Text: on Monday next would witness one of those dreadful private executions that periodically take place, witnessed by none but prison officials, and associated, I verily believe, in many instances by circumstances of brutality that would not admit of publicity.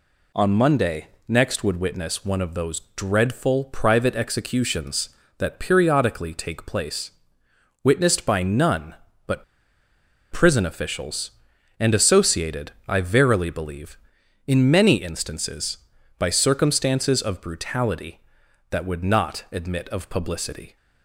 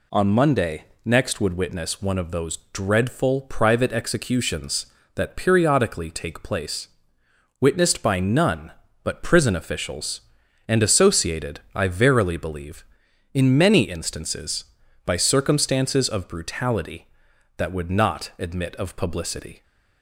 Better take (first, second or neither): second